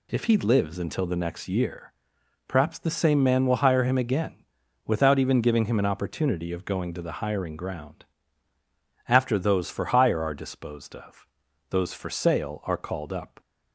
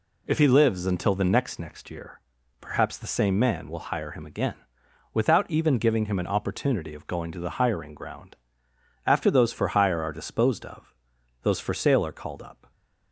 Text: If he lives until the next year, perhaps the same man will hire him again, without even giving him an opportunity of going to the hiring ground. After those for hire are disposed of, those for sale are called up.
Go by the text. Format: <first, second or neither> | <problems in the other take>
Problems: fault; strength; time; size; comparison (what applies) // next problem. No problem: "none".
first | says "next" twice; at 1.5 s